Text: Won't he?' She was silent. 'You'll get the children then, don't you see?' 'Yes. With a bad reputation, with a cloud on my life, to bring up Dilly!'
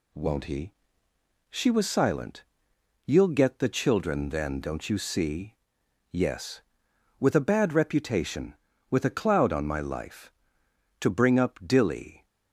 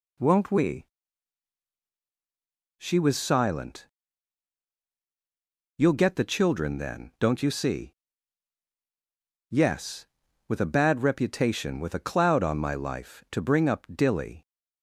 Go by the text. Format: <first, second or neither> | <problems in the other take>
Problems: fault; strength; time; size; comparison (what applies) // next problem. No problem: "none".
first | says "we" for "he"; at 0.5 s